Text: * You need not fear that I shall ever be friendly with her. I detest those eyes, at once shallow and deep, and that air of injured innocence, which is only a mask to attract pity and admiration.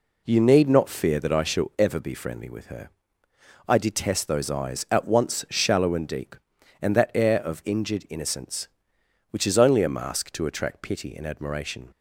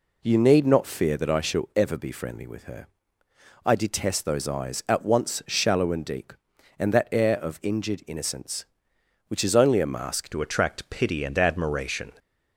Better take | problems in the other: first | changes voice at "to"; from 10.2 s on; 1.9 s long

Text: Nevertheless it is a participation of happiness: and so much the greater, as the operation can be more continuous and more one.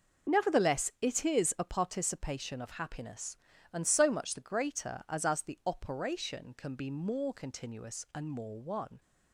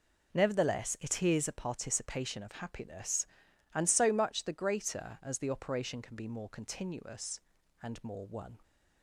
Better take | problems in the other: second | says "as" twice; at 5.2 s

